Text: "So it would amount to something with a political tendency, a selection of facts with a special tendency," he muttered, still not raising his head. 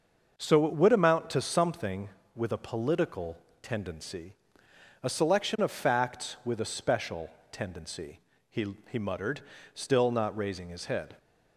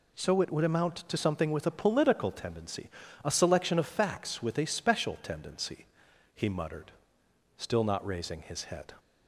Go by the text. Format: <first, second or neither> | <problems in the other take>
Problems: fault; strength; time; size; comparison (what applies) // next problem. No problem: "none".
second | starts louder than the rest; until 1.4 s; 6.5 dB // pauses between "political" and "tendency"; slight; at 3.3 s; 0.26 s long // pauses between "special" and "tendency"; slight; at 7.2 s; 0.22 s long // says "he" twice; at 8.8 s